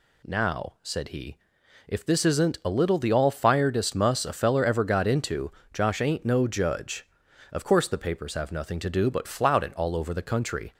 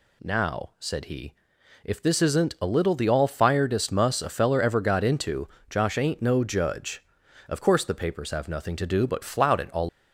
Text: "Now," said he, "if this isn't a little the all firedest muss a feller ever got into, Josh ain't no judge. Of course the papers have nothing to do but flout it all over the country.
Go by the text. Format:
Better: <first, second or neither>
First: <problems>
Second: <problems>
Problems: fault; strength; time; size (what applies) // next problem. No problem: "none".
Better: first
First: none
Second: stops before "over the country"; at 9.8 s